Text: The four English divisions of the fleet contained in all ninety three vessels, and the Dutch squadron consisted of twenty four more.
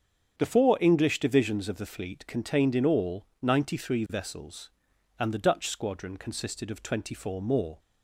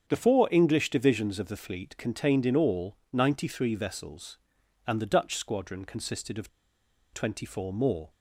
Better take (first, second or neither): first